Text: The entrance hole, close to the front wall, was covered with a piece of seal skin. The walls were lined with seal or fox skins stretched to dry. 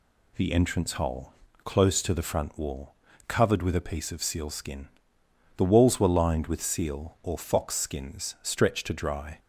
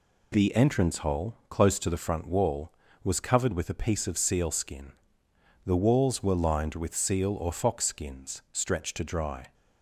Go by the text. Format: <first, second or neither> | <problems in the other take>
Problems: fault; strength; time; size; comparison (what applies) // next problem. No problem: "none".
second | skips "was"; at 3.1 s